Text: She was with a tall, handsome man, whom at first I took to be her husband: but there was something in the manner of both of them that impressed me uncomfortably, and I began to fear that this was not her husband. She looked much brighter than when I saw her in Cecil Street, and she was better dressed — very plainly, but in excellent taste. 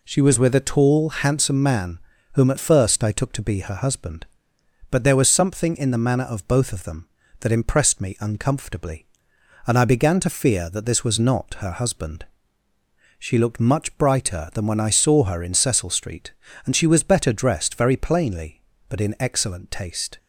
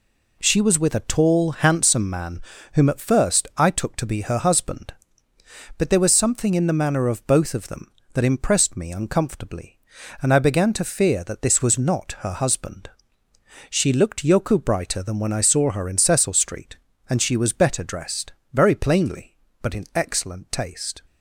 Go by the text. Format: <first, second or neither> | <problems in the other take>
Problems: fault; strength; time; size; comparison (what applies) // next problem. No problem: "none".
first | says "yoku" for "much"; at 14.2 s